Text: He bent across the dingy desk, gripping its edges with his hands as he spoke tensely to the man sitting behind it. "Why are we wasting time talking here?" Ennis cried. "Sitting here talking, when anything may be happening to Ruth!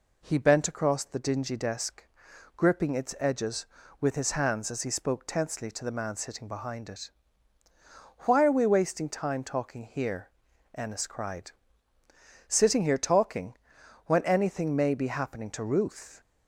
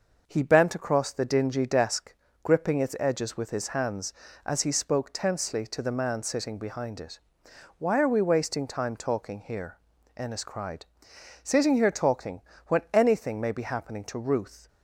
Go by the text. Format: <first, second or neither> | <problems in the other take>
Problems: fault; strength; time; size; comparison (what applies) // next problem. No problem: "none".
first | gets quieter; slight; throughout; 3 dB